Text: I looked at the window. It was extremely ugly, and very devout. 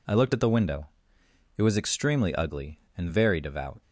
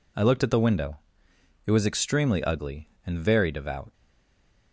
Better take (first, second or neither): first